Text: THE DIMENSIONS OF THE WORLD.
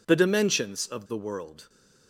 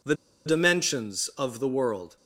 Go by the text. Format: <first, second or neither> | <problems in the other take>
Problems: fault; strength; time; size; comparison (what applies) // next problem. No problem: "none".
first | pauses between "THE" and "DIMENSIONS"; slight; at 0.1 s; 0.29 s long